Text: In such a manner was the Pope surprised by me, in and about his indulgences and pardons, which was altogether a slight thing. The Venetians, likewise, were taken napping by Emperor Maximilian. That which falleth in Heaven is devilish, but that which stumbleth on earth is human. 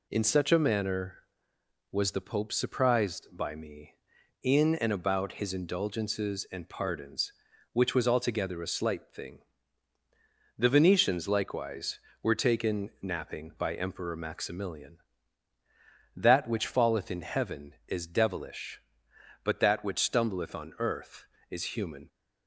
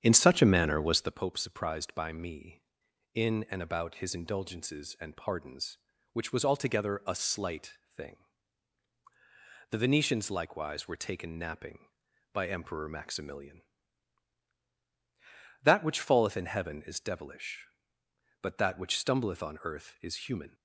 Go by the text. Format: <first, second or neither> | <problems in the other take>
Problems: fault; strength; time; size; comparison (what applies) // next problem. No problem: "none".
first | starts louder than the rest; strong; until 1.3 s; 8.5 dB // pauses between "slight" and "thing"; slight; at 7.7 s; 0.18 s long